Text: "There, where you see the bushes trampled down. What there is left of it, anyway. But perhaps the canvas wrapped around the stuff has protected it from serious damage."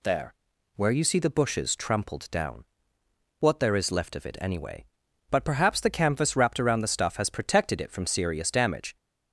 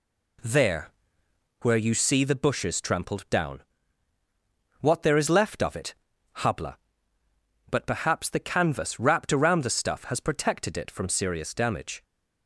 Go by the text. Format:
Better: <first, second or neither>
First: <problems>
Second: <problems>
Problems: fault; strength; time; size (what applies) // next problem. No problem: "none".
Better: first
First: none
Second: says "habla" for "anyway"; at 6.3 s